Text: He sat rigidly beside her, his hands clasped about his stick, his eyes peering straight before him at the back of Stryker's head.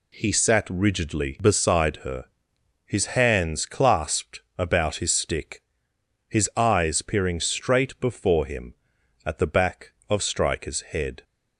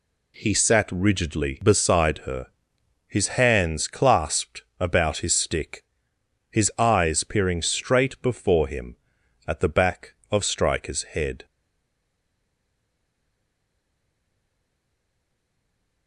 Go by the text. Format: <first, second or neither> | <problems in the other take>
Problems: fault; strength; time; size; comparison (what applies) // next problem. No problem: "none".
first | pauses between "clasped" and "about"; slight; at 4.6 s; 0.18 s long; slight in the first // stays silent after the last word; strong; from 11.4 s on; 4.6 s long